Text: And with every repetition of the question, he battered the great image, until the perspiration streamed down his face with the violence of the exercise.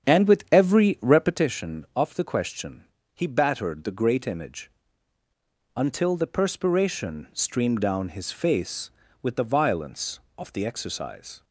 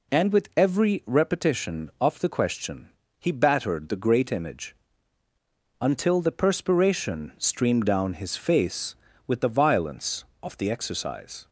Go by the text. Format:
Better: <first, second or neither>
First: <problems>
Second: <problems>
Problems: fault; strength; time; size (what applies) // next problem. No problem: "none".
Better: second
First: starts louder than the rest; strong; until 1.5 s; 8.5 dB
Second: none